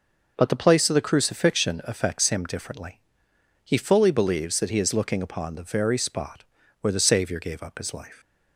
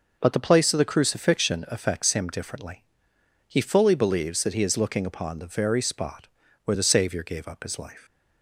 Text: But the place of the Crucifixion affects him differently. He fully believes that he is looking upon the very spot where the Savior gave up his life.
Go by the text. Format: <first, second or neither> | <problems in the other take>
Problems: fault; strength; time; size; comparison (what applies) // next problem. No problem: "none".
neither | pauses between "spot" and "where"; the same in both